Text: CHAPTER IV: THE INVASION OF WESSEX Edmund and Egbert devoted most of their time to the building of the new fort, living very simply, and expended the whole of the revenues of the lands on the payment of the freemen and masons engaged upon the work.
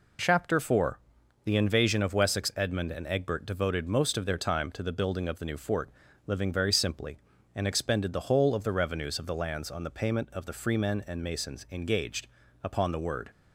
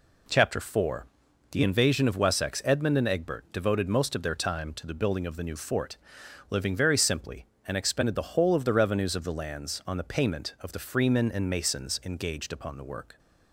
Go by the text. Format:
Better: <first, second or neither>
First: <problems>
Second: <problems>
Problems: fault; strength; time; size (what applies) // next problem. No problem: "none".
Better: second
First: pauses between "engaged" and "upon"; slight; at 12.2 s; 0.34 s long // says "word" for "work"; at 12.9 s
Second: none